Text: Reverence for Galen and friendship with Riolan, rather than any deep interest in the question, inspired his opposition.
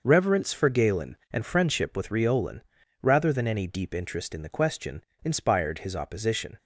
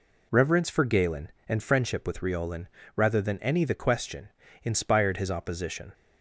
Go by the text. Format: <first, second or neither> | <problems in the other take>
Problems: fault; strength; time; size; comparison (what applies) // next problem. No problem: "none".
first | skips "deep interest in"; at 3.6 s